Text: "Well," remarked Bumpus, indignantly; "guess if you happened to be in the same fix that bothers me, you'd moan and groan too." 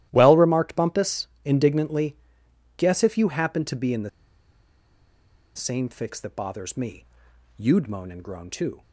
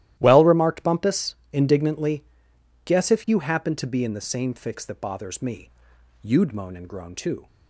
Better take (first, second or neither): second